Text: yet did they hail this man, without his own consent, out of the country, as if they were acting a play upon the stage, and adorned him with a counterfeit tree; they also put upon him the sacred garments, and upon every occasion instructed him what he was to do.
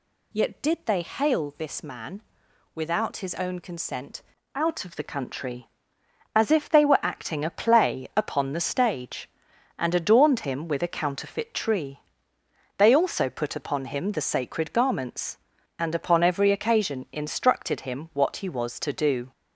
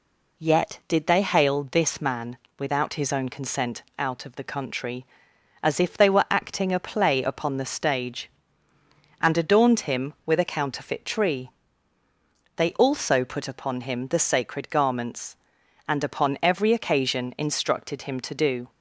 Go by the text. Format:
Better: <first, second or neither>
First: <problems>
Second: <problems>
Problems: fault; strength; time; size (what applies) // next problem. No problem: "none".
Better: first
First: none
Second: skips "what he was"; at 18.1 s